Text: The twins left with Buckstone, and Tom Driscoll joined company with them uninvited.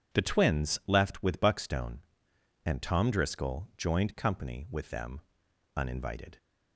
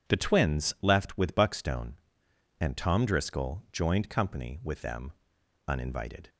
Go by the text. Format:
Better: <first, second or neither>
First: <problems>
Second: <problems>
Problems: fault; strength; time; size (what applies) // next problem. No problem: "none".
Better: neither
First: pauses between "them" and "uninvited"; noticeable; at 5.2 s; 0.54 s long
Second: pauses between "them" and "uninvited"; noticeable; at 5.1 s; 0.54 s long